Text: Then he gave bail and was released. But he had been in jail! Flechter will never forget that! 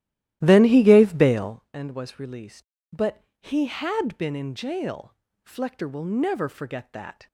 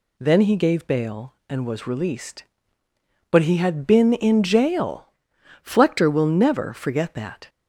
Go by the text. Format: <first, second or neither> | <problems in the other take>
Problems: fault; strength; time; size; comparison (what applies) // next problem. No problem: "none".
second | starts louder than the rest; strong; until 1.6 s; 14 dB // pauses between "But" and "he"; slight; at 3.2 s; 0.20 s long